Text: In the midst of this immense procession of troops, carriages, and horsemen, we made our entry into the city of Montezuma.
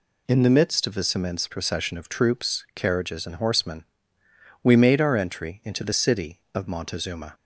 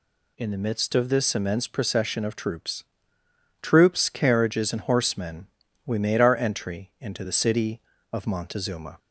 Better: first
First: none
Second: says "troops" twice; at 3.6 s

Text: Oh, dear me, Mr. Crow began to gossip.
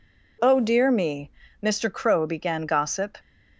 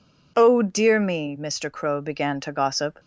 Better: second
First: skips "to"; at 2.6 s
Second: none

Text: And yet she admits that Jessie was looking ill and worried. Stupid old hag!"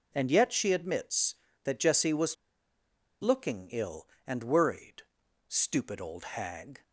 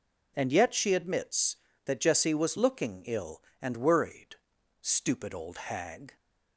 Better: second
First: pauses between "was" and "looking"; noticeable; at 2.3 s; 0.87 s long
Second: none

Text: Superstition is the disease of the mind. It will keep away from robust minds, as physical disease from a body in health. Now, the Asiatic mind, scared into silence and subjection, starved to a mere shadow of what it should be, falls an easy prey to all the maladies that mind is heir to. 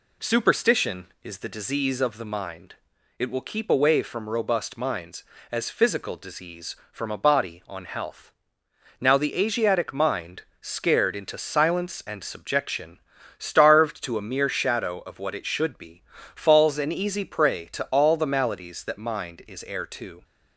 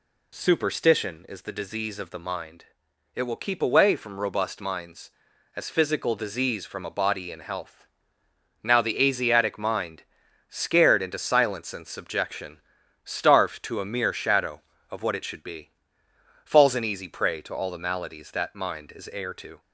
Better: second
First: says "on" for "in"; at 7.6 s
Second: none

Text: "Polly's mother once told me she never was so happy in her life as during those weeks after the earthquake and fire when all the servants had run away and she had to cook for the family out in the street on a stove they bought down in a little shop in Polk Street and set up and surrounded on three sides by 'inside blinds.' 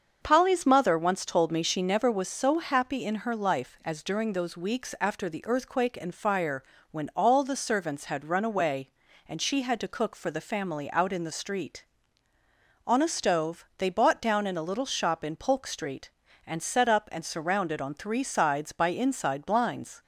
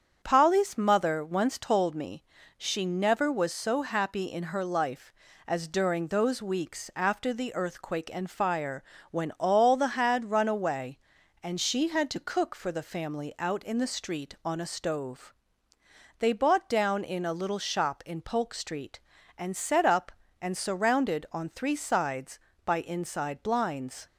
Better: first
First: starts louder than the rest; until 1.2 s; 6.5 dB // pauses between "fire" and "when"; slight; at 6.6 s; 0.30 s long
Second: starts louder than the rest; strong; until 1.2 s; 7.5 dB // pauses between "me" and "she"; slight; at 2.2 s; 0.34 s long // pauses between "fire" and "when"; slight; at 8.8 s; 0.26 s long // skips "servants"; at 9.9 s // pauses between "stove" and "they"; noticeable; at 15.3 s; 0.86 s long

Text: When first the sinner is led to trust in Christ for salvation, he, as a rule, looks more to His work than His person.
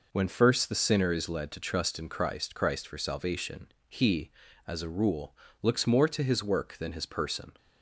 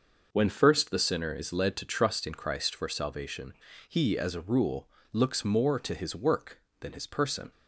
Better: second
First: says "Christ" twice; at 2.5 s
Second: none

